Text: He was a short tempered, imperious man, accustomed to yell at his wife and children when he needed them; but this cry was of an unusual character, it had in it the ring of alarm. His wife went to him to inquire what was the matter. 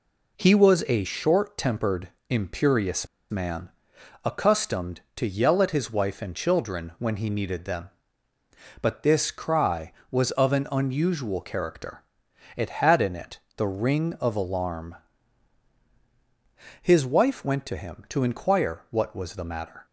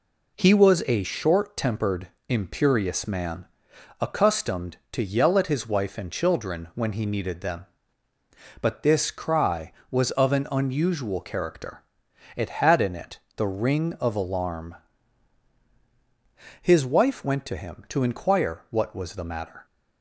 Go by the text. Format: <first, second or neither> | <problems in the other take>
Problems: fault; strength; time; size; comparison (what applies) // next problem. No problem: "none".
second | pauses between "imperious" and "man"; slight; at 3.0 s; 0.24 s long // pauses between "it" and "the"; slight; at 13.3 s; 0.16 s long; slight in the second